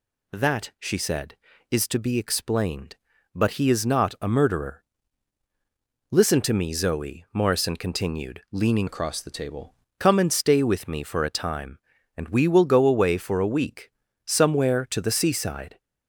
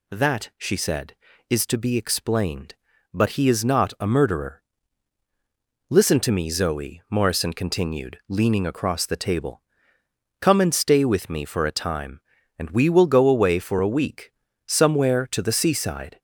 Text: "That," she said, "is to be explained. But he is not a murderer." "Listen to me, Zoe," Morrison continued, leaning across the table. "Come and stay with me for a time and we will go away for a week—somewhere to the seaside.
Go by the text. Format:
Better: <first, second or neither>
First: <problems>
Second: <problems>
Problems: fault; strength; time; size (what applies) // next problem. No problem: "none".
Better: second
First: changes voice from "across" to "table"; from 8.8 to 9.7 s; 0.9 s long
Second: none